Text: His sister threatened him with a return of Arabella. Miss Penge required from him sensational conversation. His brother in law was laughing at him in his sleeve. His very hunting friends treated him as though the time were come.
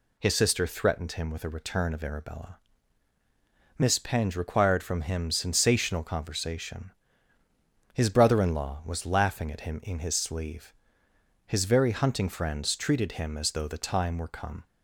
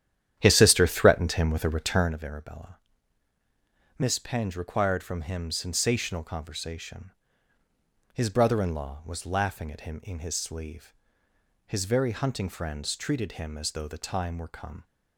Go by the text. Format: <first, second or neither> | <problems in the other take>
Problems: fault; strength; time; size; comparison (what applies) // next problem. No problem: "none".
first | starts louder than the rest; strong; until 2.2 s; 10.5 dB